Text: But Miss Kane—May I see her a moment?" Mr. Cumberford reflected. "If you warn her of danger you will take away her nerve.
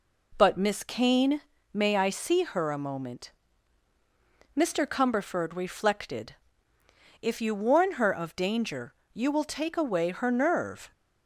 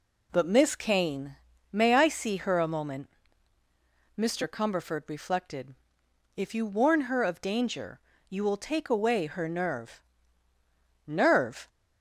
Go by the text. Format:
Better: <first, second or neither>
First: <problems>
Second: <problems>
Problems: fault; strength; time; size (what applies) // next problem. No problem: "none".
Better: first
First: pauses between "danger" and "you"; slight; at 8.9 s; 0.18 s long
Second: pauses between "danger" and "you"; slight; at 7.9 s; 0.30 s long // says "nerve" twice; at 11.0 s